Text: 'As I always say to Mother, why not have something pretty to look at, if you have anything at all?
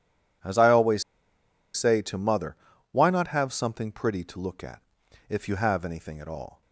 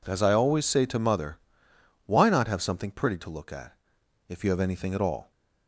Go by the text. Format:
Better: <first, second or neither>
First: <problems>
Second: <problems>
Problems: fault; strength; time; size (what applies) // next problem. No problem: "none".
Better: second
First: pauses between "always" and "say"; noticeable; at 1.0 s; 0.74 s long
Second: none